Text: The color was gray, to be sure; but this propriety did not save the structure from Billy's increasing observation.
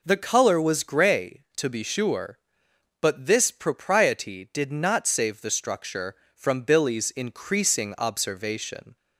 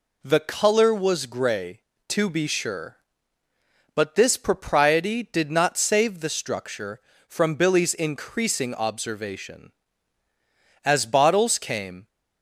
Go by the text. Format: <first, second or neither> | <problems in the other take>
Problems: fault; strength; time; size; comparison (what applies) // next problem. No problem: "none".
first | goes on to say "As bottles came"; noticeable; from 10.8 s on; 1.2 s long